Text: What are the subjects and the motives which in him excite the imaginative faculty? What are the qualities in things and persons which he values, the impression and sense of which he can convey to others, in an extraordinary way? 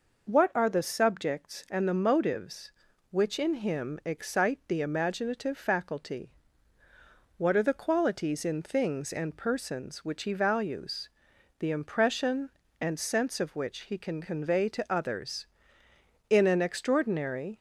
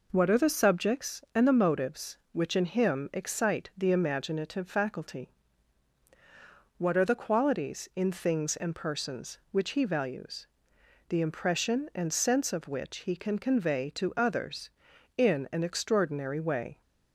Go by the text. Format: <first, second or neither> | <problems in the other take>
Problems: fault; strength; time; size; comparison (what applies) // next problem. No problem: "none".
second | stops before "way"; at 17.5 s